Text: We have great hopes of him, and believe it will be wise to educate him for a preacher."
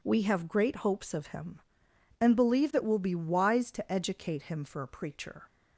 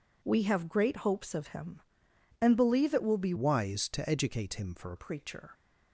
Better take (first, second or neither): first